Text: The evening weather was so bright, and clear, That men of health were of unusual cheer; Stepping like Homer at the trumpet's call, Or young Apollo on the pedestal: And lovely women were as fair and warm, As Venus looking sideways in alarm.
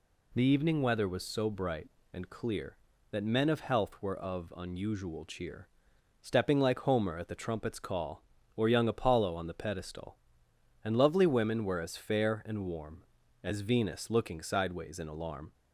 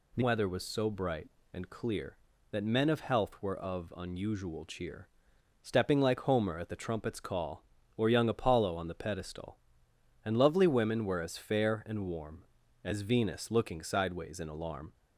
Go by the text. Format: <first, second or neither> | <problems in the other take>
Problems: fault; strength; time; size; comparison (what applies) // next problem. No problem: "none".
first | skips "evening"; at 0.2 s